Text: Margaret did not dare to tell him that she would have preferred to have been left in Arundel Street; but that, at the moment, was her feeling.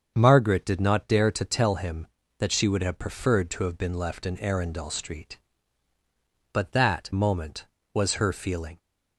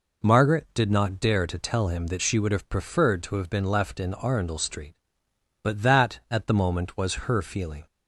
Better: second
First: starts louder than the rest; until 1.1 s; 7 dB // skips "at the"; at 7.1 s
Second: none

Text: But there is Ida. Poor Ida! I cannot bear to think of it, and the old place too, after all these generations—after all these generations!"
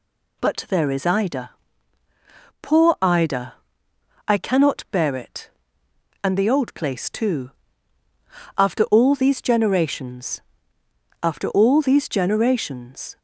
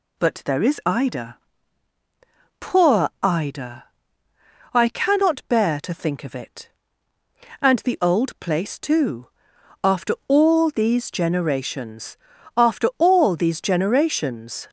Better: second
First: skips "to think of"; at 5.1 s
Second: none

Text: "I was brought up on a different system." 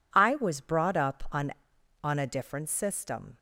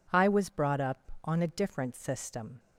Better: second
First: says "on" twice; at 2.0 s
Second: none

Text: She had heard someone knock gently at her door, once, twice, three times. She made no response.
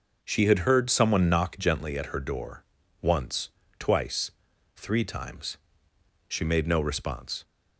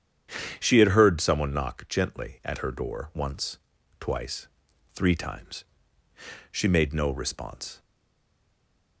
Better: first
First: none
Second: starts louder than the rest; strong; until 1.6 s; 8.5 dB // stays silent after the last word; noticeable; from 7.7 s on; 1.3 s long

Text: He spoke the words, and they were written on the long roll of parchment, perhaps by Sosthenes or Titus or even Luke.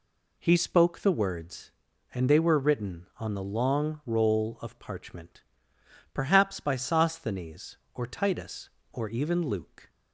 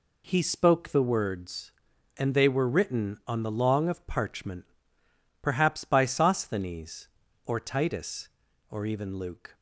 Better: first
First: none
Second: skips "roll"; at 3.8 s

